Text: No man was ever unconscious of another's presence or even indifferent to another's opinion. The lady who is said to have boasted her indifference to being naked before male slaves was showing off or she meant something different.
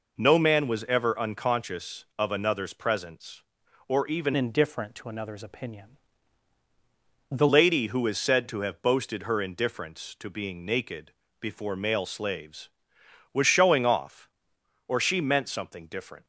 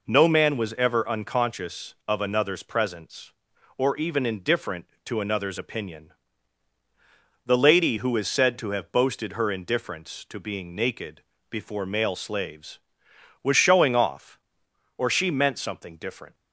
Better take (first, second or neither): second